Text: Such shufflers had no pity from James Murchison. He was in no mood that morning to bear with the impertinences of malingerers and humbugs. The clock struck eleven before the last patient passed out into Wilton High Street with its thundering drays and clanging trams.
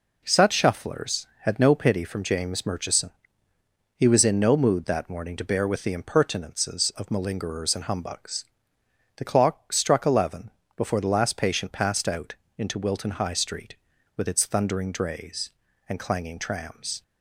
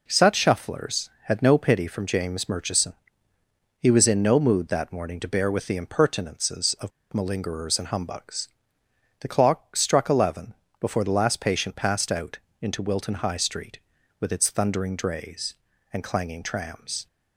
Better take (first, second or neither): first